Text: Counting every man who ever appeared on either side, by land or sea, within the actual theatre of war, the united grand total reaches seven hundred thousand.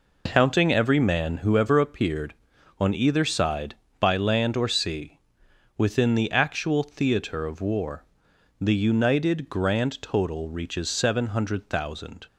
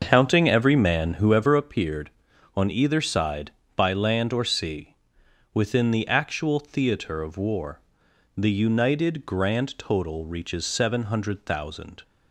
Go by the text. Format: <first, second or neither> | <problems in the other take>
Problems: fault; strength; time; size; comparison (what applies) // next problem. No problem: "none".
first | starts louder than the rest; until 1.6 s; 6.5 dB